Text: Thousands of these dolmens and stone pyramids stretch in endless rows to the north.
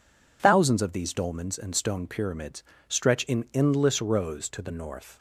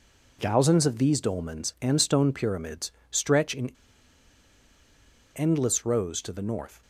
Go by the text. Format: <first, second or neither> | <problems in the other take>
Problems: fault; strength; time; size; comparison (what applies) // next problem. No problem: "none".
first | pauses between "pyramids" and "stretch"; slight; at 2.9 s; 0.18 s long; slight in the first // pauses between "in" and "endless"; strong; at 3.7 s; 1.6 s long